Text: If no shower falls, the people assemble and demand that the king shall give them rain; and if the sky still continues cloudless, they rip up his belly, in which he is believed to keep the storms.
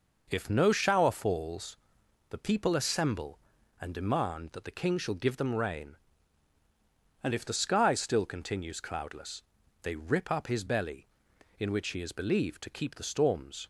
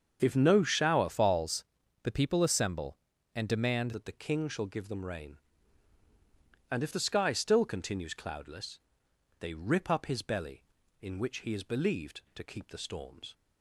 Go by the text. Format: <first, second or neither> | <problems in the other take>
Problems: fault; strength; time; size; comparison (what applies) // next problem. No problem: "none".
first | starts louder than the rest; strong; until 1.2 s; 7 dB // changes voice from "falls" to "demand"; from 1.1 to 3.9 s; 2.8 s long